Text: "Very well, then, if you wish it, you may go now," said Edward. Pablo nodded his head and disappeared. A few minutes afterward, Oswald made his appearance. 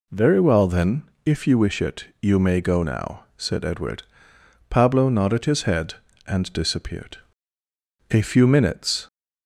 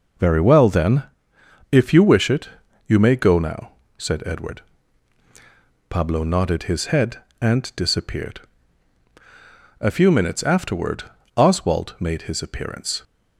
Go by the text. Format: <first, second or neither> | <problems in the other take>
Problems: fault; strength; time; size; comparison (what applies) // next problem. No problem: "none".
second | stops before "afterward Oswald made his appearance"; at 9.0 s